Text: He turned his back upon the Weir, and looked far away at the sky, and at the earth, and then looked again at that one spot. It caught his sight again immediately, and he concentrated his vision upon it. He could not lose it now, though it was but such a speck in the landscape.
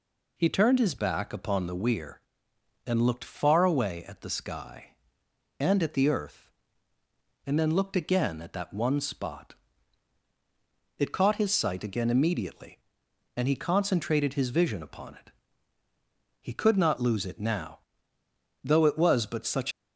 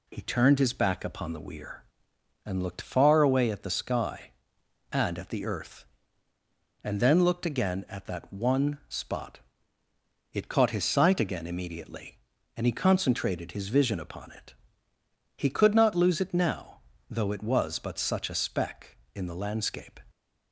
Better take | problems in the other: second | stops before "a speck in the landscape"; at 19.7 s

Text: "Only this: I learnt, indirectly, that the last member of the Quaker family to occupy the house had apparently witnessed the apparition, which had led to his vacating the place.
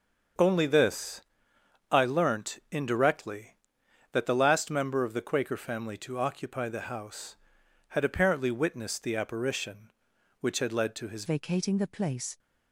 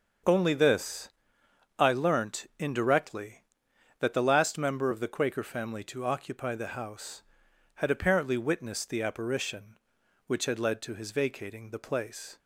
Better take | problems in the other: second | starts louder than the rest; until 2.0 s; 7 dB; also in the second // changes voice at "vacating"; from 11.2 s on; 1.1 s long

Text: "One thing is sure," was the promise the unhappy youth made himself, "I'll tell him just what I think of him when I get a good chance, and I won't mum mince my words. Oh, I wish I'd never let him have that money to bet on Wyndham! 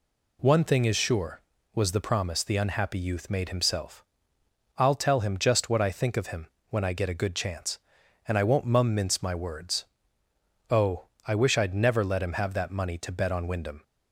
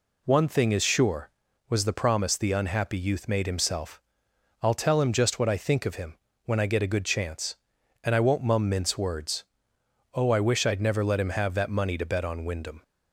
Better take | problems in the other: first | pauses between "him" and "when"; slight; at 6.1 s; 0.28 s long; slight in the first // skips "my"; at 8.9 s

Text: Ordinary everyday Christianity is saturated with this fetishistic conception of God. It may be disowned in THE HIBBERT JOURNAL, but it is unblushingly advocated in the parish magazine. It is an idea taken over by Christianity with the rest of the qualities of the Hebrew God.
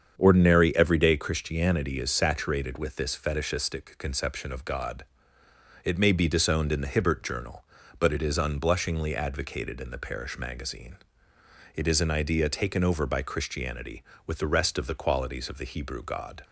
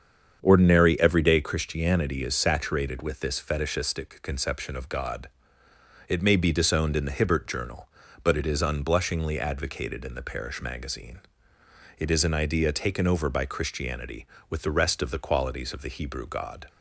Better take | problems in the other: neither | starts louder than the rest; strong; the same in both

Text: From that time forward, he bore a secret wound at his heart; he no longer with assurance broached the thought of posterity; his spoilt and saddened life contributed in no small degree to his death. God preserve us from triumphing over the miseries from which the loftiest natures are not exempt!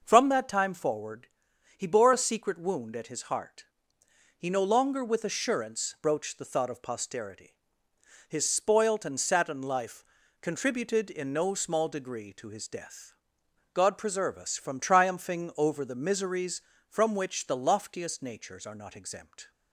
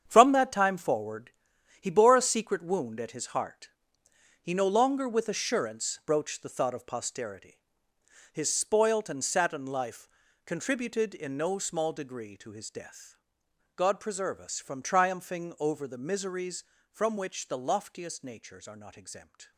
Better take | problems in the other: first | gets quieter; strong; throughout; 10 dB // pauses between "life" and "contributed"; slight; at 10.0 s; 0.36 s long; slight in the first

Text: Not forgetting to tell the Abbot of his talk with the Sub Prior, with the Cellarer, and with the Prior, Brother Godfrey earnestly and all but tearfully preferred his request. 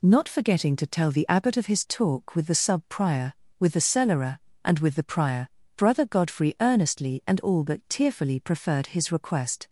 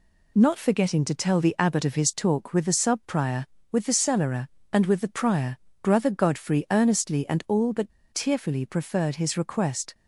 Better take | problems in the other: first | pauses between "but" and "tearfully"; slight; at 7.9 s; 0.25 s long

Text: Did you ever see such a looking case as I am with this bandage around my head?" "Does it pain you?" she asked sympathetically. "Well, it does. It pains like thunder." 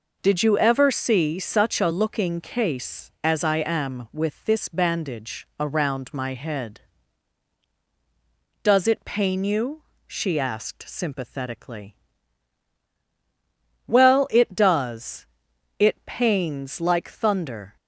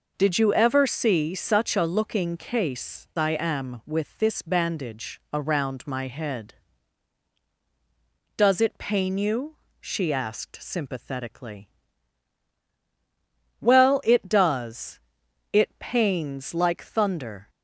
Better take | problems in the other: first | skips "as"; at 3.1 s

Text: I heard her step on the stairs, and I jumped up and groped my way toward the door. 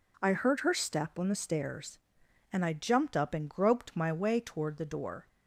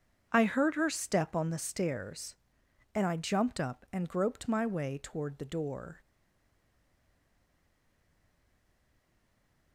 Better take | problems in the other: first | starts louder than the rest; strong; until 1.3 s; 7.5 dB // stays silent after the last word; strong; from 6.0 s on; 3.7 s long

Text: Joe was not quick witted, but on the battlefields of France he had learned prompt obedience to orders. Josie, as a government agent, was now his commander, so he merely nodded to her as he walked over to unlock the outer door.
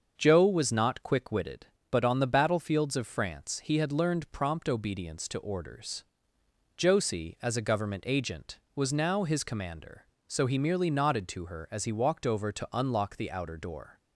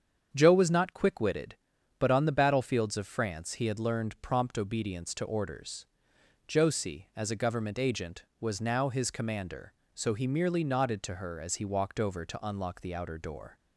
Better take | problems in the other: neither | starts louder than the rest; the same in both

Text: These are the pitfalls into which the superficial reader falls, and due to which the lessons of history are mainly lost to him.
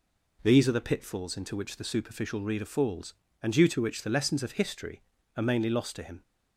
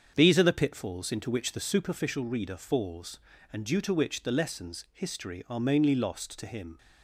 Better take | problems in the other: first | starts louder than the rest; strong; until 1.1 s; 7.5 dB // skips "of"; at 4.8 s

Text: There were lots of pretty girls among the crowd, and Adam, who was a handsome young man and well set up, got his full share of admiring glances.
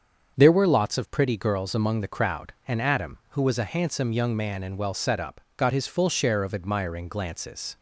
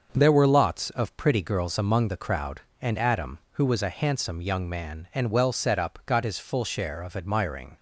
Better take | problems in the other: first | starts louder than the rest; until 1.1 s; 6.5 dB; also in the first // stops before "glances"; at 7.7 s

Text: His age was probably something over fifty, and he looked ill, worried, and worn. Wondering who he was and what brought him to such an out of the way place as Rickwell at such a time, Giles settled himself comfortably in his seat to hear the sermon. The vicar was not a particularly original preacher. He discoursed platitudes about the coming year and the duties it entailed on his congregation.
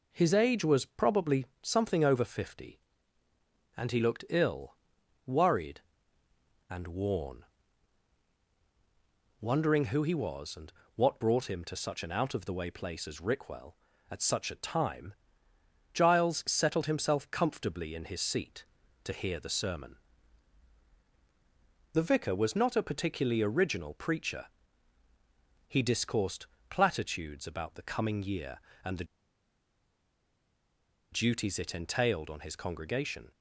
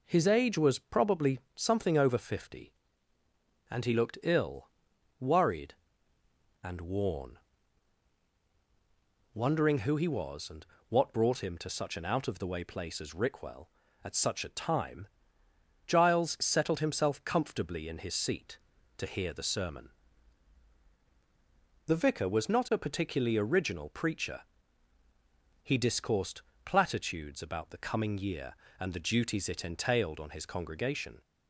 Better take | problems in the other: second | pauses between "probably" and "something"; slight; at 1.4 s; 0.16 s long; slight in the second // pauses between "and" and "what"; slight; at 10.7 s; 0.24 s long; slight in the second // pauses between "discoursed" and "platitudes"; slight; at 26.4 s; 0.24 s long; slight in the second // pauses between "the" and "duties"; strong; at 29.0 s; 2.0 s long

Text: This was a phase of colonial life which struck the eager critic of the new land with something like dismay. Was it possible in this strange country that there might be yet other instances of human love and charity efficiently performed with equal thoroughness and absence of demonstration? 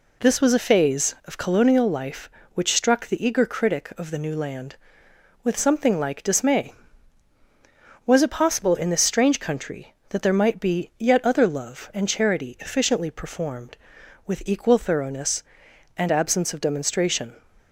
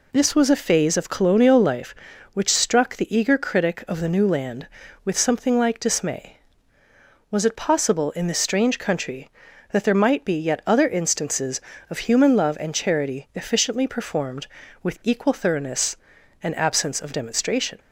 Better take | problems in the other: second | skips "instances of human"; at 11.4 s

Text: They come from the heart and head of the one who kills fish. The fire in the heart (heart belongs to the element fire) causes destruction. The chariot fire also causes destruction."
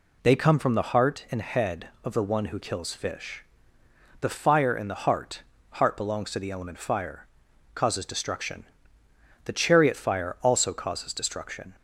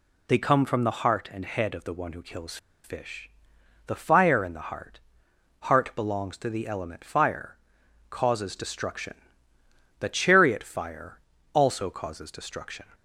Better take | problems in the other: first | pauses between "kills" and "fish"; slight; at 2.5 s; 0.27 s long // pauses between "fire" and "also"; slight; at 11.1 s; 0.34 s long

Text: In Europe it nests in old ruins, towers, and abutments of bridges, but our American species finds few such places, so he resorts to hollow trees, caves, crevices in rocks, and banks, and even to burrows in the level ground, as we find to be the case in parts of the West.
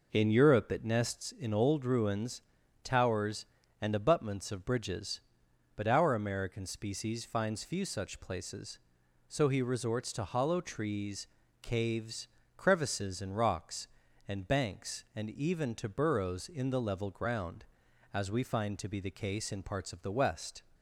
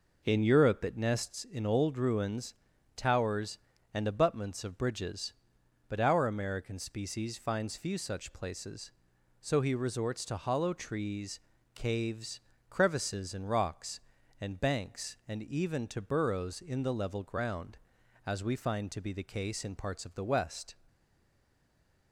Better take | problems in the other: first | stays silent after the last word; noticeable; from 20.8 s on; 1.3 s long

